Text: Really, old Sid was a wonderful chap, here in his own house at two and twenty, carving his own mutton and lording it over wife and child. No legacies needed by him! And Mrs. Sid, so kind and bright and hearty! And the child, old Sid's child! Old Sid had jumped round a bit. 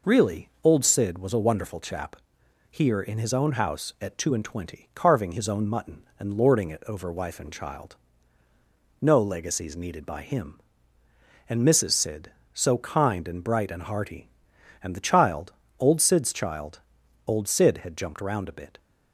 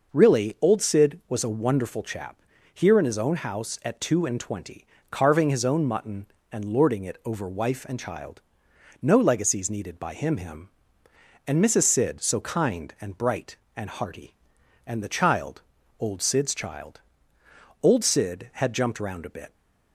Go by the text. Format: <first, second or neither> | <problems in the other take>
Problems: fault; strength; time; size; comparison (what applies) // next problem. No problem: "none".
first | says "him" twice; at 10.3 s